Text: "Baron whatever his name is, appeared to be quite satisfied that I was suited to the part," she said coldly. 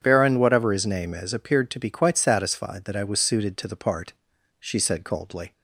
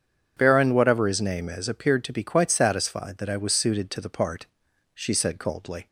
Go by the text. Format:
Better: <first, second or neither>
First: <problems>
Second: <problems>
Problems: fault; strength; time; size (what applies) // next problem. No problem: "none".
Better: neither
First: starts louder than the rest; strong; until 1.0 s; 8 dB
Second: starts louder than the rest; strong; until 1.3 s; 8 dB